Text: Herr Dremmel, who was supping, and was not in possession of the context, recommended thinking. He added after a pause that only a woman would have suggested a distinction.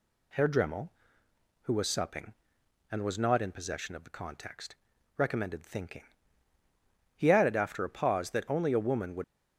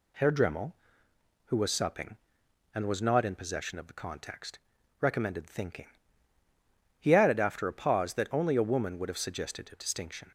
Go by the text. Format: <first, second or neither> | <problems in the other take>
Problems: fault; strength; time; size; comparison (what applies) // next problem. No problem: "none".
second | stops before "have suggested a distinction"; at 9.2 s